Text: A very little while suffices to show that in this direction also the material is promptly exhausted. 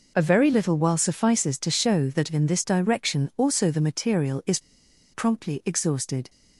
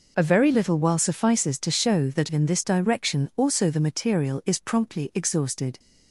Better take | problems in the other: second | pauses between "is" and "promptly"; noticeable; at 4.5 s; 0.52 s long

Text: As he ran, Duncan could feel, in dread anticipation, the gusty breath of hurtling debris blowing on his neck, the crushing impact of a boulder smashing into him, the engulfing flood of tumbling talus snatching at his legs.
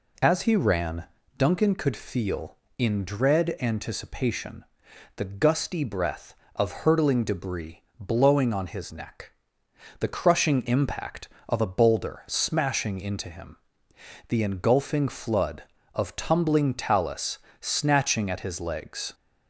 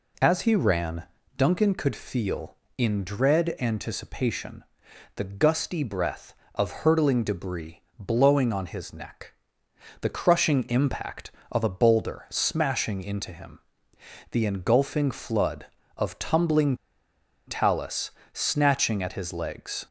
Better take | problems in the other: first | pauses between "debris" and "blowing"; slight; at 7.8 s; 0.16 s long; slight in the first // pauses between "tumbling" and "talus"; noticeable; at 16.7 s; 0.70 s long // pauses between "talus" and "snatching"; slight; at 18.1 s; 0.22 s long; slight in the first

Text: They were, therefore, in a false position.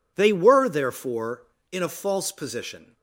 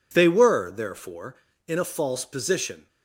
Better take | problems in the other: neither | none

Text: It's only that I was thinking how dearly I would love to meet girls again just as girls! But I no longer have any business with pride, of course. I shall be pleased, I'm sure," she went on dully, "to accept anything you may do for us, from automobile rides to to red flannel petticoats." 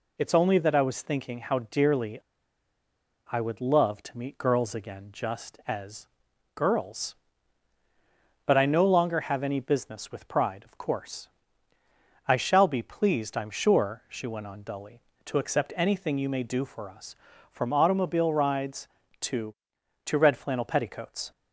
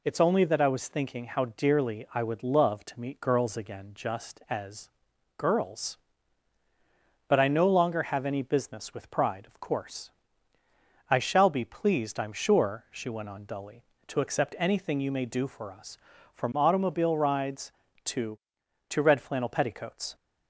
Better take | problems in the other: second | pauses between "dearly" and "I"; at 2.1 s; 1.1 s long // pauses between "as" and "girls"; noticeable; at 6.0 s; 0.46 s long; noticeable in the second

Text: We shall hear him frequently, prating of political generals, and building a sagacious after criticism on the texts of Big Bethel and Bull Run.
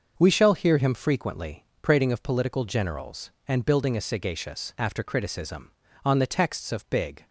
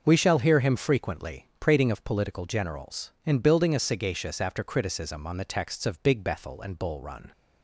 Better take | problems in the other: second | starts louder than the rest; noticeable; until 1.1 s; 6 dB; noticeable in the second // stops before "Bethel and Bull Run"; at 7.2 s

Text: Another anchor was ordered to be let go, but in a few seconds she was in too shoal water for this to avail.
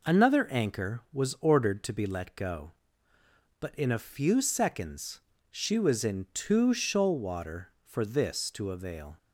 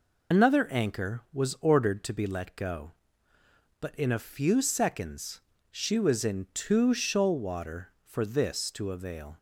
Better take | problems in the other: first | loses the start of "Another"; at 0.3 s; 60 ms // pauses between "seconds" and "she"; slight; at 5.3 s; 0.32 s long; slight in the first

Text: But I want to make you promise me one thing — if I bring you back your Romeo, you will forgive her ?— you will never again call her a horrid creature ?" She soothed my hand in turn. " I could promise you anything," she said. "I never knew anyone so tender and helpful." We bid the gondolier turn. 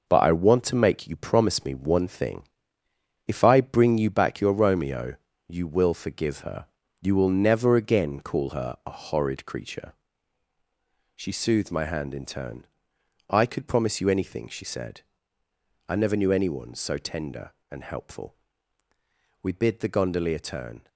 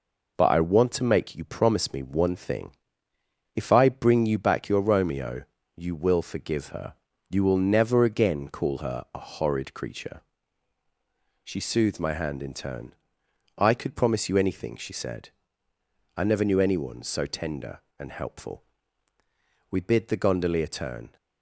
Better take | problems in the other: second | gets quieter; strong; throughout; 9 dB

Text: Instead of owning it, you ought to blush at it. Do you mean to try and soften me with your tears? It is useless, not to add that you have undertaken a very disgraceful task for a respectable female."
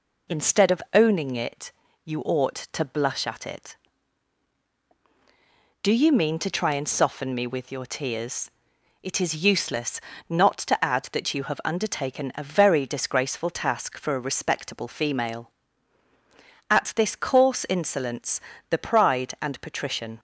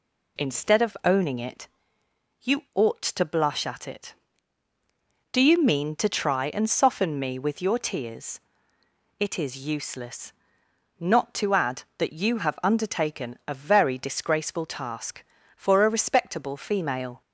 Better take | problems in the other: second | goes on to say "At this coarse insolence the pride and patrician"; strong; from 16.6 s on; 3.5 s long

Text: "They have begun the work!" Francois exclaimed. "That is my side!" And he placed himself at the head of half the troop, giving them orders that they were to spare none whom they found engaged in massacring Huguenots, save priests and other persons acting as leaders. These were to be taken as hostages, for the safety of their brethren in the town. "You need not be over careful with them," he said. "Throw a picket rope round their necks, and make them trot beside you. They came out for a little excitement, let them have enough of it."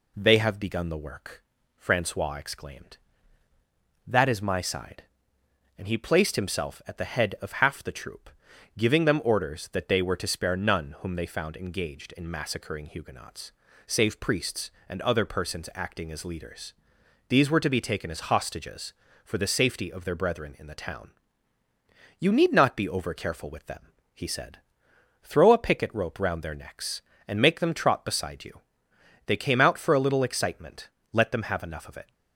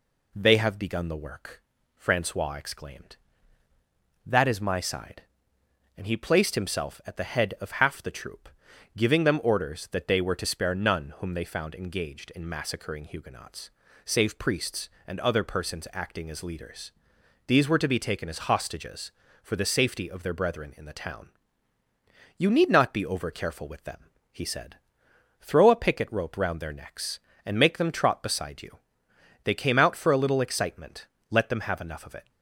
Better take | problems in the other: neither | none

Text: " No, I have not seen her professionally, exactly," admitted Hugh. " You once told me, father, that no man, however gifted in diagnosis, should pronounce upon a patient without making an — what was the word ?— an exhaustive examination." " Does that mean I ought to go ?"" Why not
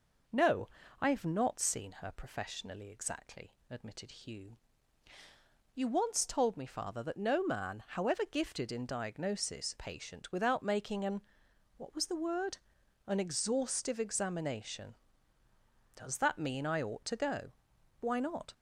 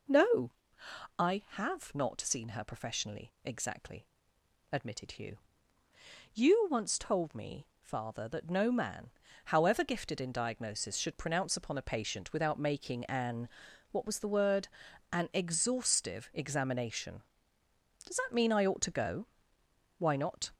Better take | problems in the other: second | skips "should pronounce upon a"; at 9.7 s

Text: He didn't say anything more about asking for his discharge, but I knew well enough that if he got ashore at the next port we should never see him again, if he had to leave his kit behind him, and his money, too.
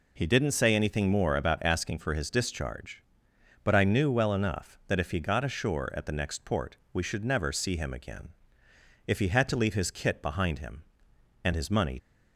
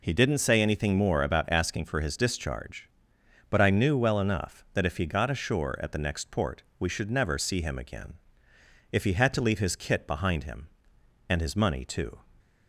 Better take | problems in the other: second | pauses between "port" and "we"; slight; at 6.7 s; 0.18 s long; slight in the second // stops before "too"; at 11.9 s

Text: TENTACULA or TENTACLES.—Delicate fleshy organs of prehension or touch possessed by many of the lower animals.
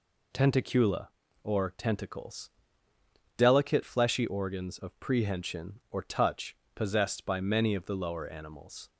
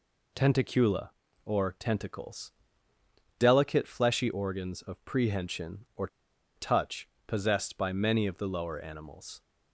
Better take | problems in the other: first | pauses between "or" and "touch"; noticeable; at 6.0 s; 0.49 s long // pauses between "touch" and "possessed"; slight; at 7.0 s; 0.22 s long; slight in the first

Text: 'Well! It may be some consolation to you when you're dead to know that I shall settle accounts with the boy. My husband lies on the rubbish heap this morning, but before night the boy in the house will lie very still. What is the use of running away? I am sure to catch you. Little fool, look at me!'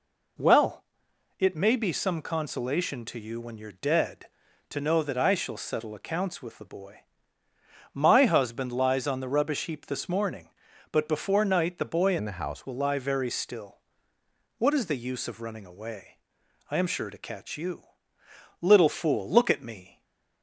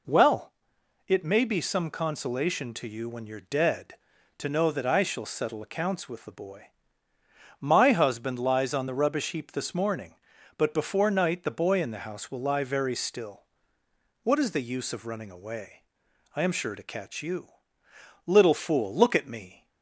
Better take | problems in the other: second | changes voice from "in" to "house"; from 12.1 to 12.6 s; 0.5 s long // stays silent after the last word; slight; from 19.8 s on; 0.6 s long

